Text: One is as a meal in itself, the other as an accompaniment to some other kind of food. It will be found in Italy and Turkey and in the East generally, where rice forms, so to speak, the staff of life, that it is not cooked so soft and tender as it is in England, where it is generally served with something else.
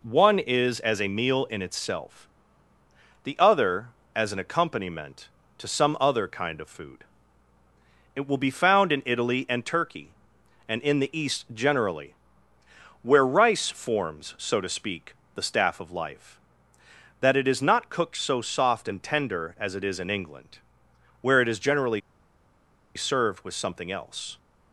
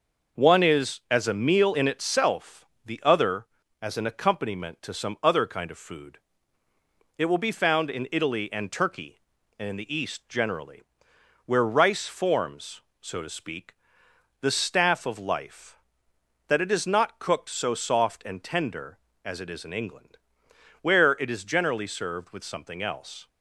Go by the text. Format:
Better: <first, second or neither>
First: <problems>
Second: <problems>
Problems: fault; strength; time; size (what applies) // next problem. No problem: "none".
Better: second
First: pauses between "generally" and "served"; noticeable; at 22.0 s; 0.95 s long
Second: none